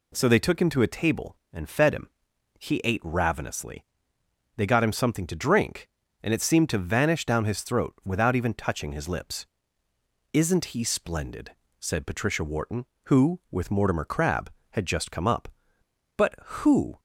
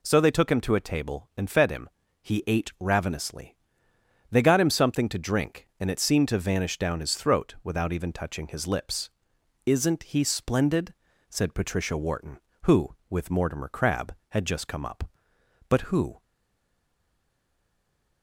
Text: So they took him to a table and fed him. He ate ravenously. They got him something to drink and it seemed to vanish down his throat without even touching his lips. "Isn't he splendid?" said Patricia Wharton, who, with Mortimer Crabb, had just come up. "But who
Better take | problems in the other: first | stays silent after the last word; noticeable; from 16.2 s on; 2.0 s long

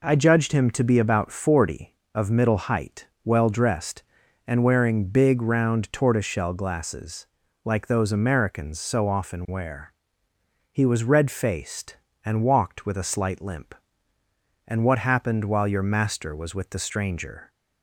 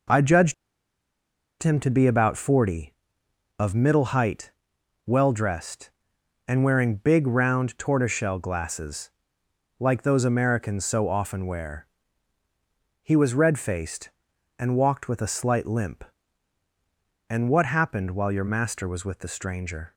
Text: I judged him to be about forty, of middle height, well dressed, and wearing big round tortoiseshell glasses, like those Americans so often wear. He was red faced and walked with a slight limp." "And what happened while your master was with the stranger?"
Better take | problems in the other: first | pauses between "judged" and "him"; at 0.5 s; 1.0 s long

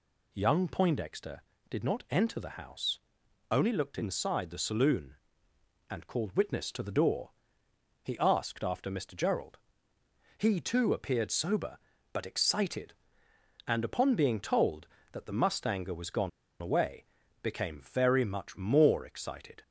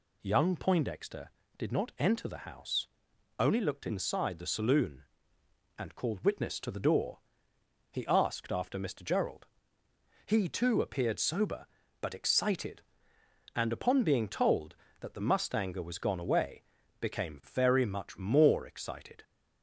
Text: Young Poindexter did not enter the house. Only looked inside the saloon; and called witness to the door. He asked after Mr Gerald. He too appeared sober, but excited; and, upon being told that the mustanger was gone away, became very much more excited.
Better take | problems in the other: second | pauses between "gone" and "away"; slight; at 16.2 s; 0.32 s long

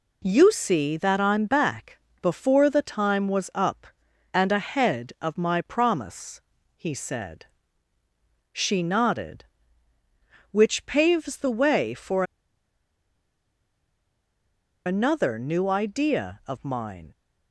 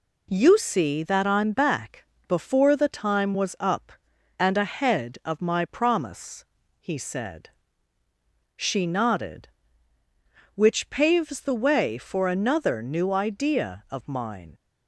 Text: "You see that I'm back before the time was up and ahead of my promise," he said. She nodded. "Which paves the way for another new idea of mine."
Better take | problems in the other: second | pauses between "back" and "before"; slight; at 1.9 s; 0.22 s long; slight in the second // pauses between "for" and "another"; strong; at 12.2 s; 2.6 s long

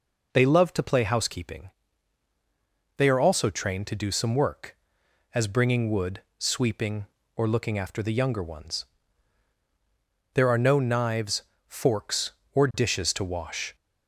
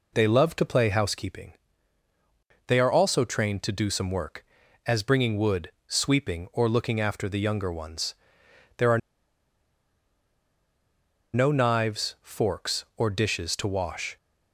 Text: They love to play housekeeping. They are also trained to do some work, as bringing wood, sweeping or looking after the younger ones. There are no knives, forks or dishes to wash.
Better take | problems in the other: first | pauses between "are" and "no"; strong; at 8.9 s; 2.3 s long

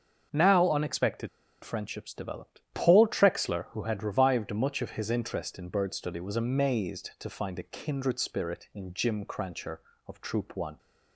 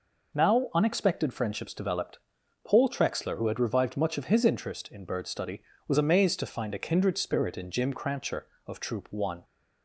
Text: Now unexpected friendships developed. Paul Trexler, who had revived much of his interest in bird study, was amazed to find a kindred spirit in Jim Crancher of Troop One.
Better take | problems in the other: second | starts louder than the rest; until 1.6 s; 7 dB // pauses between "unexpected" and "friendships"; slight; at 1.2 s; 0.34 s long

